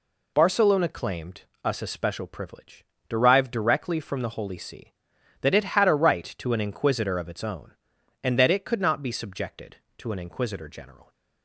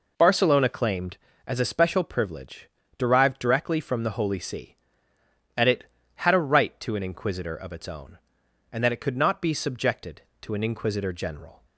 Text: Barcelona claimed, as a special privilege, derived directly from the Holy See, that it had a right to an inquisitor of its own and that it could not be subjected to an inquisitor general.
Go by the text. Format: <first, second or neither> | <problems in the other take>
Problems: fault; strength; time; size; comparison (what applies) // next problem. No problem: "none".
second | says "us" for "as"; at 1.6 s